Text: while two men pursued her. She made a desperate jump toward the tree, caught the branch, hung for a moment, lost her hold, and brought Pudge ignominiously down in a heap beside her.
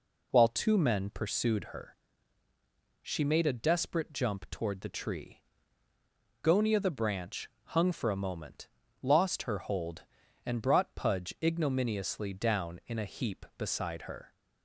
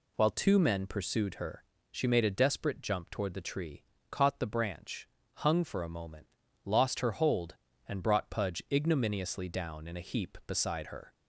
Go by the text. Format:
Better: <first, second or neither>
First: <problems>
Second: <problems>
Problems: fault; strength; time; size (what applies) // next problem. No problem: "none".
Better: second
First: says "gonia" for "caught"; at 6.4 s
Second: none